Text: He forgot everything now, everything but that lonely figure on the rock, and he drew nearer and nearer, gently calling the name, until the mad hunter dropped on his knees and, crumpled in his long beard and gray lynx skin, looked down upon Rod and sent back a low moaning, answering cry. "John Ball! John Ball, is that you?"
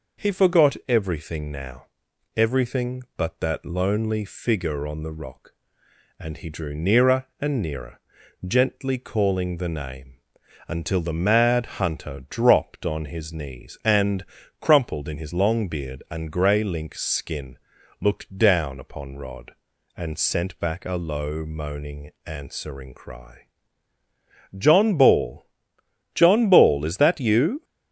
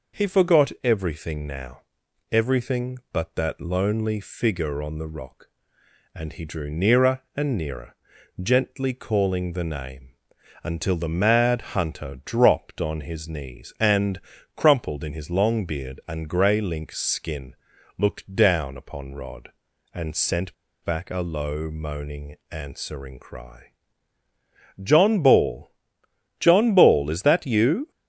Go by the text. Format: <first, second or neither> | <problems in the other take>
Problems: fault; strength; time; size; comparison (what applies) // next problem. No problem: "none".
first | pauses between "sent" and "back"; slight; at 20.5 s; 0.29 s long